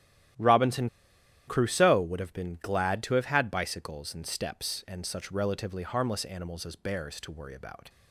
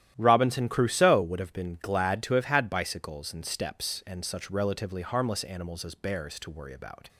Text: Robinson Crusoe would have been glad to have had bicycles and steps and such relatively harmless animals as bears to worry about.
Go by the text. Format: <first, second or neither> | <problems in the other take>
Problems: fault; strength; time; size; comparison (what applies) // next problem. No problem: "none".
second | starts louder than the rest; strong; until 1.9 s; 12.5 dB; strong in the second // pauses between "Robinson" and "Crusoe"; noticeable; at 0.8 s; 0.58 s long